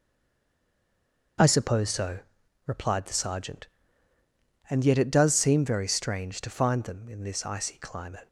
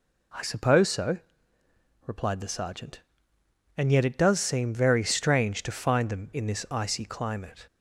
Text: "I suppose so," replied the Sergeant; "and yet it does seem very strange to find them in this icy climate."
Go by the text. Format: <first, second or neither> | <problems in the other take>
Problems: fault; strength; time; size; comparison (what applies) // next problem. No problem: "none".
second | stays silent before the first word; noticeable; until 1.3 s; 1.3 s long